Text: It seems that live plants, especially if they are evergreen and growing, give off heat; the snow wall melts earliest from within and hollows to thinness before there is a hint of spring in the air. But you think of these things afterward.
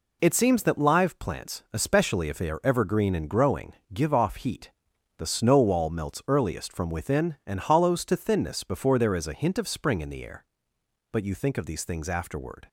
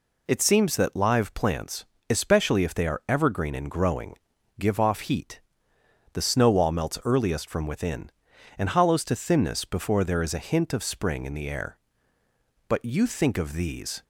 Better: first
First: none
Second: stops before "things afterward"; at 14.0 s

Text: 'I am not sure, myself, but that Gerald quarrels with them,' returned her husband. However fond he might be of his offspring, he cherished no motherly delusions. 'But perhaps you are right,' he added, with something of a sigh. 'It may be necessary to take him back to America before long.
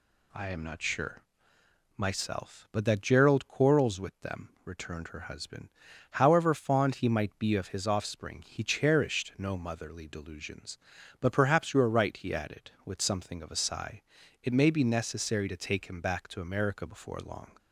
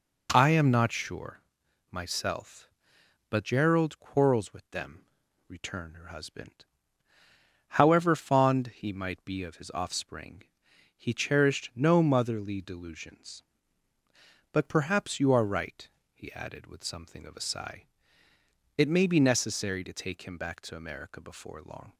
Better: first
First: none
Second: skips "that"; at 3.4 s

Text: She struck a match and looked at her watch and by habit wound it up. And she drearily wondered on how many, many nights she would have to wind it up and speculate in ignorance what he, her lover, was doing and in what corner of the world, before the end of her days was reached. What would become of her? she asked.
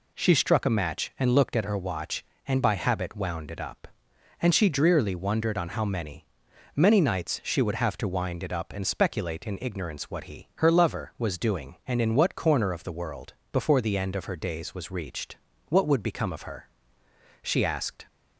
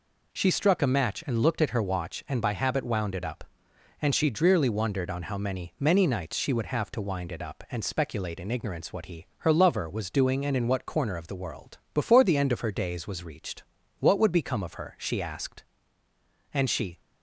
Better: first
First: none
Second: goes on to say "And she"; slight; from 16.5 s on; 0.48 s long

